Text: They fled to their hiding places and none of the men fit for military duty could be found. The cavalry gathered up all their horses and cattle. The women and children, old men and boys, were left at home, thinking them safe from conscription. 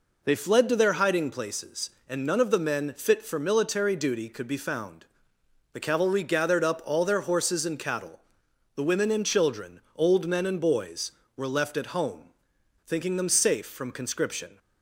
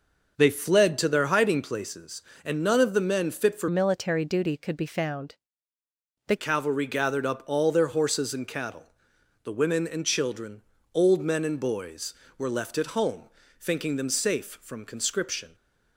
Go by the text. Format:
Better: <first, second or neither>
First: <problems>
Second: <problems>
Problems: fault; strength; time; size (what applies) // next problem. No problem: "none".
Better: first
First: none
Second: changes voice from "military" to "The"; from 3.6 to 6.3 s; 2.7 s long